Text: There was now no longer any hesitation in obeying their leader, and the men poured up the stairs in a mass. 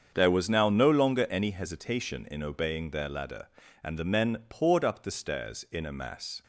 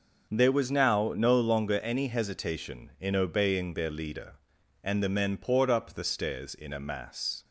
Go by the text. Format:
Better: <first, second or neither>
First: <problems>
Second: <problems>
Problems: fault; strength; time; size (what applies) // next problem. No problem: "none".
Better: second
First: starts louder than the rest; strong; until 1.1 s; 7 dB // says "ladder" for "leader"; at 3.0 s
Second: starts louder than the rest; noticeable; until 1.3 s; 6 dB